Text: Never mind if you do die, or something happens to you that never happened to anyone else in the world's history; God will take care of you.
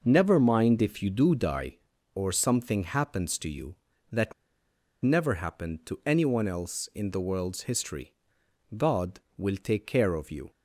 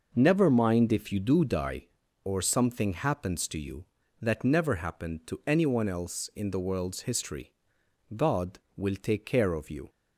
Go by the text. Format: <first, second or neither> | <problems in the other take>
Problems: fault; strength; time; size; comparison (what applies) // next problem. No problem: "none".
second | pauses between "that" and "never"; noticeable; at 4.3 s; 0.68 s long